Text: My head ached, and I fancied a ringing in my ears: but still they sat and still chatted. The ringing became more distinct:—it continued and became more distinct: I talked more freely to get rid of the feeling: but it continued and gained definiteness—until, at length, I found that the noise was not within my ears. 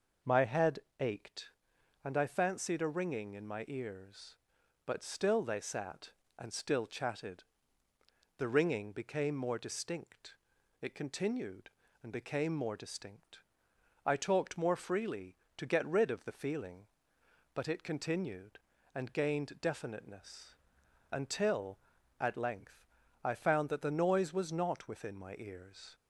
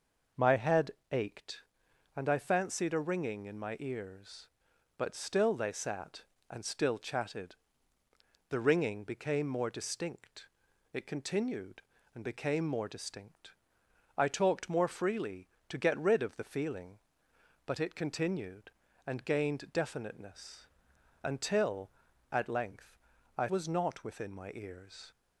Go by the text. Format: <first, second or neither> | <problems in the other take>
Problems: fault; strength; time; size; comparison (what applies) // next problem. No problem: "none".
first | pauses between "head" and "ached"; slight; at 0.9 s; 0.18 s long; slight in the first // skips "found that the noise"; at 23.4 s